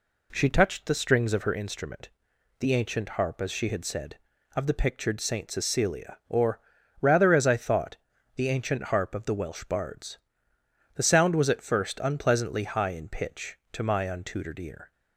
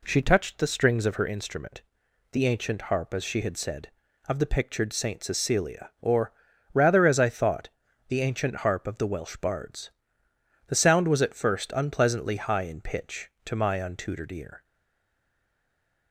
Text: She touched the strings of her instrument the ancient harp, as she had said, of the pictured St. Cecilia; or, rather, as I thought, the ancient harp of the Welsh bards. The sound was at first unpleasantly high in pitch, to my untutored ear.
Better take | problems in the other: first | pauses between "instrument" and "the"; noticeable; at 1.8 s; 0.50 s long; noticeable in the first // stays silent after the last word; noticeable; from 14.6 s on; 1.4 s long

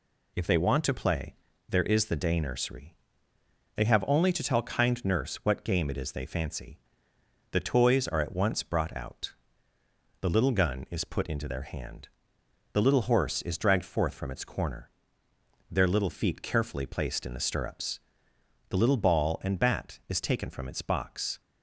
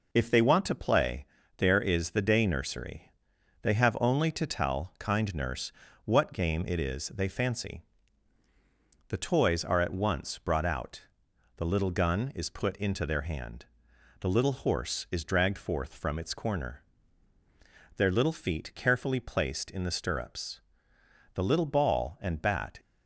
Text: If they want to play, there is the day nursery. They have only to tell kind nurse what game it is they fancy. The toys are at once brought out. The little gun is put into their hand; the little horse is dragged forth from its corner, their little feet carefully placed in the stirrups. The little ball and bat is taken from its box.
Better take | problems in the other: first | pauses between "nurse" and "what"; slight; at 5.7 s; 0.34 s long // stops before "is taken from its box"; at 22.7 s

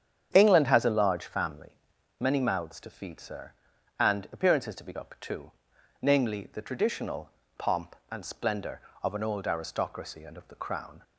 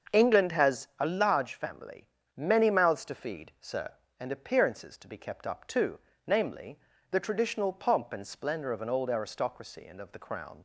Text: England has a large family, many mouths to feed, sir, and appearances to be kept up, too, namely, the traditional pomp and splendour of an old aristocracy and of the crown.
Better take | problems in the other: second | starts louder than the rest; strong; until 1.3 s; 8.5 dB; also in the second // skips "kept"; at 4.9 s // pauses between "traditional" and "pomp"; slight; at 7.2 s; 0.30 s long

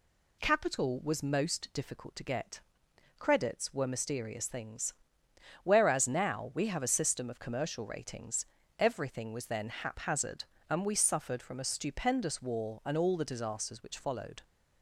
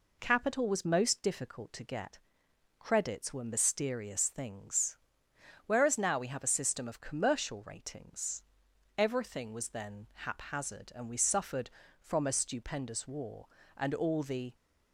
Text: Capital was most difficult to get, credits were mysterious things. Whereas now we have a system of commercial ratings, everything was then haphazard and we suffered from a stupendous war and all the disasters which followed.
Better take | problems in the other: first | stops before "disasters which followed"; at 14.5 s

